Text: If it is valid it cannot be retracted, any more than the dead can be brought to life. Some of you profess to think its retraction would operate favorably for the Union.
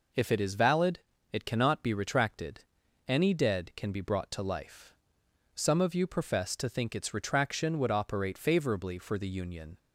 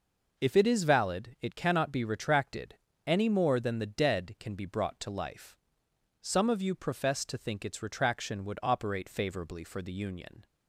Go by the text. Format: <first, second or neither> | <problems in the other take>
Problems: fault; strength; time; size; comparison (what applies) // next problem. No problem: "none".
second | pauses between "valid" and "it"; slight; at 0.9 s; 0.32 s long // skips "more than the"; at 3.3 s